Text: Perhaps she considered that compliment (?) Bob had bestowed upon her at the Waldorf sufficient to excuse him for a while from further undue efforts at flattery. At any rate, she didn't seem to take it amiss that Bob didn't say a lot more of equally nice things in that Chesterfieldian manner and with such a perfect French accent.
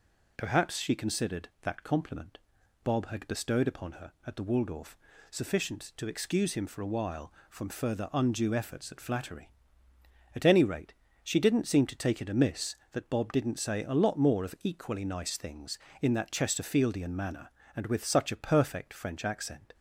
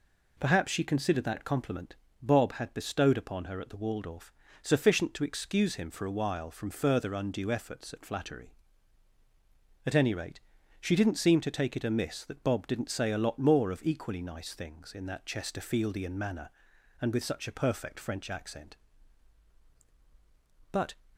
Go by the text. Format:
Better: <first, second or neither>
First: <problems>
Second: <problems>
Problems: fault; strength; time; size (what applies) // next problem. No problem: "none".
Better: first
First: pauses between "Waldorf" and "sufficient"; slight; at 4.9 s; 0.34 s long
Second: pauses between "Waldorf" and "sufficient"; slight; at 4.3 s; 0.30 s long // goes on to say "But"; slight; from 20.7 s on; 0.22 s long